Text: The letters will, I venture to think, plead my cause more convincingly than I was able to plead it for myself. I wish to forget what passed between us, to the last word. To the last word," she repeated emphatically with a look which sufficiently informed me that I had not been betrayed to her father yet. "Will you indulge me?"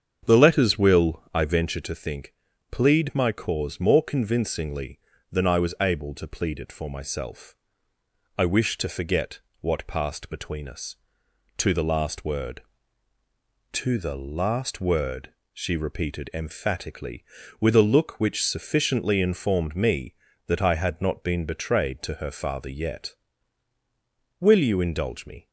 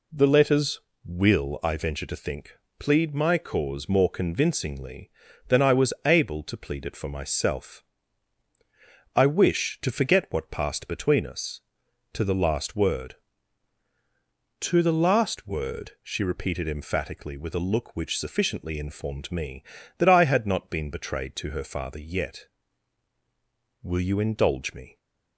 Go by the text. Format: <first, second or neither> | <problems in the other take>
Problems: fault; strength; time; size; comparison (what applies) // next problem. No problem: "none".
second | starts louder than the rest; strong; until 1.9 s; 7.5 dB // pauses between "forget" and "what"; slight; at 9.3 s; 0.20 s long